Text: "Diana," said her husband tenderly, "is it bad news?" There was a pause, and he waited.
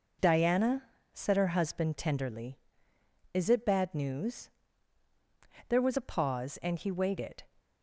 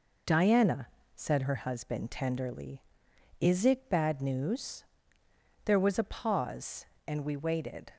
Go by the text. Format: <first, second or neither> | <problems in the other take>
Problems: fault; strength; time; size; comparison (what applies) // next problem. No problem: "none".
first | says "we" for "he"; at 7.2 s